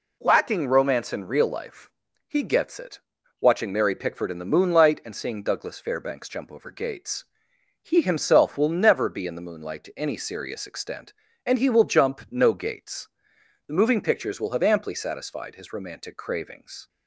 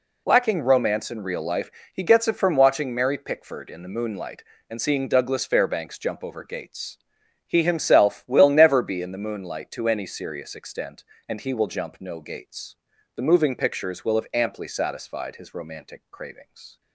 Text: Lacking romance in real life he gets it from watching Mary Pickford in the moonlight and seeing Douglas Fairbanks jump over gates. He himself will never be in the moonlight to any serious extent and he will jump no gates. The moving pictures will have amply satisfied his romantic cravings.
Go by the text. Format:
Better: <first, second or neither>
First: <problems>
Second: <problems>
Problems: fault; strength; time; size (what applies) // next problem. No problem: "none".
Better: second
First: pauses between "life" and "he"; slight; at 1.9 s; 0.36 s long // skips "from"; at 3.1 s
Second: pauses between "life" and "he"; slight; at 1.7 s; 0.24 s long